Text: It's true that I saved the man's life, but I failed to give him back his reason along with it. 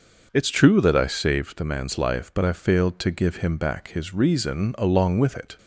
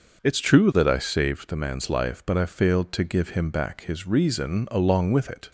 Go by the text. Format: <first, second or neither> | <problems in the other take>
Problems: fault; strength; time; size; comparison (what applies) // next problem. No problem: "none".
neither | starts louder than the rest; noticeable; the same in both